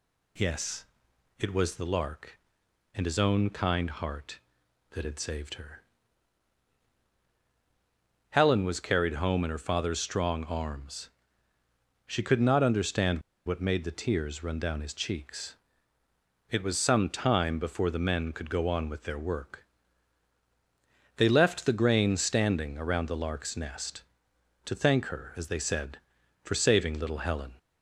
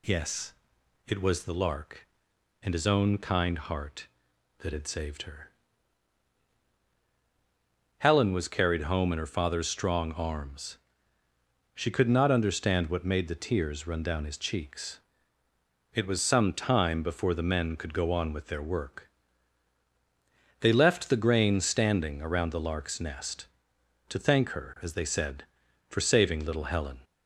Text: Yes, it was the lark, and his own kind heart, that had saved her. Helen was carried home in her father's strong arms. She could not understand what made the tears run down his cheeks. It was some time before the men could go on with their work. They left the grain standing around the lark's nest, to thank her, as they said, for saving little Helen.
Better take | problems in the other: second | pauses between "understand" and "what"; slight; at 13.2 s; 0.25 s long

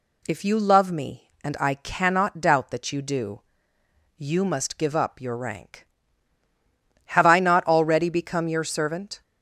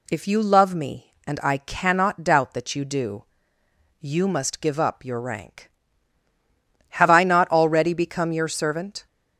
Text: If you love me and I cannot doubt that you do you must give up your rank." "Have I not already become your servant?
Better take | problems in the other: neither | pauses between "do" and "you"; noticeable; the same in both

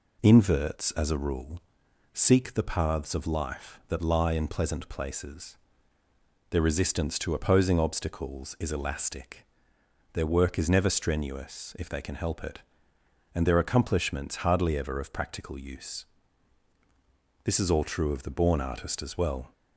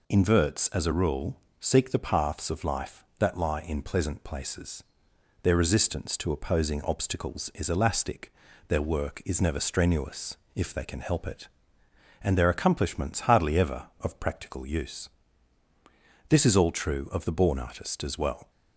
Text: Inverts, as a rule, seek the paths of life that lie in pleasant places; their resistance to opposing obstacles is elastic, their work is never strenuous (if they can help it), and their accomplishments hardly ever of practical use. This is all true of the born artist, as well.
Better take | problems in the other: neither | none

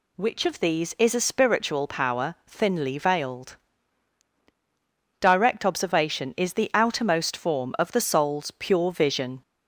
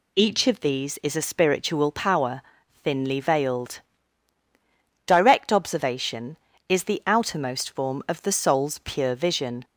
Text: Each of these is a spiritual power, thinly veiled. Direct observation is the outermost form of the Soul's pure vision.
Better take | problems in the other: second | says "Which" for "Each"; at 0.1 s

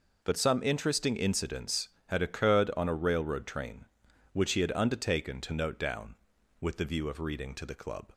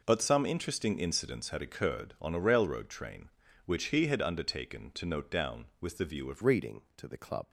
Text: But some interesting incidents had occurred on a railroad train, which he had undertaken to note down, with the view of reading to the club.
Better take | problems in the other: first | changes voice at "reading"; from 6.4 s on; 1.0 s long

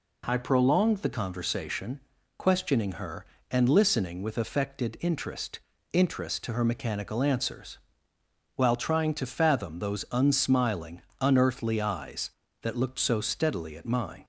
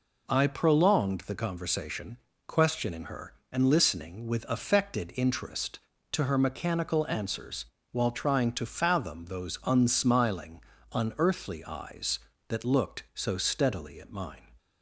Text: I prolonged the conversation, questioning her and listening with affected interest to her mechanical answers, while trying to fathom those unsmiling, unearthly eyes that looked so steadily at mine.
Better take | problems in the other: second | says "interest" twice; at 5.9 s

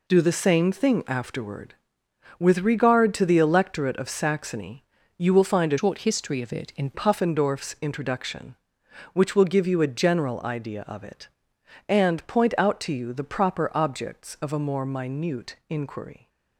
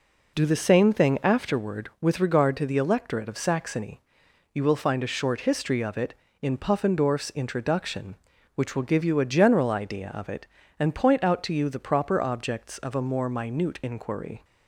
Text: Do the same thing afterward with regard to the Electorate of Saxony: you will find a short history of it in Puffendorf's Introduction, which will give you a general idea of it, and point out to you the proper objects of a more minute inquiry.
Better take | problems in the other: second | changes voice from "short" to "in"; from 5.7 to 6.8 s; 1.1 s long

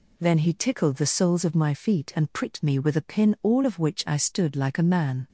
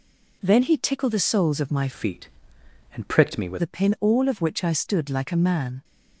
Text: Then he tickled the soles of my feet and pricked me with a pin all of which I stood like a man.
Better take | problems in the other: first | changes voice from "feet" to "with"; from 1.9 to 3.6 s; 1.7 s long

